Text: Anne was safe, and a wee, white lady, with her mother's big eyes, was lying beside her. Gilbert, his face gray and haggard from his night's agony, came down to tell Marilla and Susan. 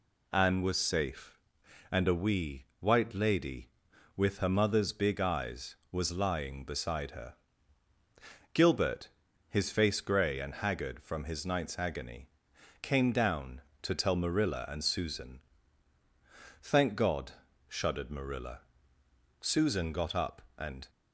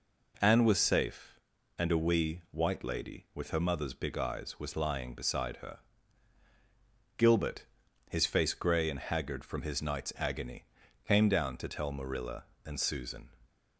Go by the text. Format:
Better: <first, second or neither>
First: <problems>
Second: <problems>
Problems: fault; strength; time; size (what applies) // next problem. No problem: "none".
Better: second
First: goes on to say "Thank God shuddered Marilla Susan got up and"; strong; from 16.6 s on; 4.2 s long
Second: none